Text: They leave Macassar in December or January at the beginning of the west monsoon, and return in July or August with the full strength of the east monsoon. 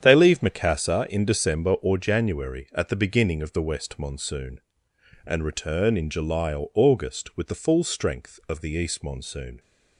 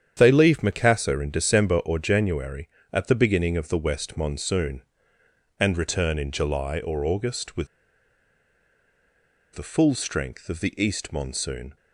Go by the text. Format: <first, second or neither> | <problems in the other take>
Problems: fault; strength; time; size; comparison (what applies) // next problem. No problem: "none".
first | starts louder than the rest; strong; until 1.1 s; 8.5 dB; strong in the first // pauses between "with" and "the"; strong; at 7.6 s; 1.8 s long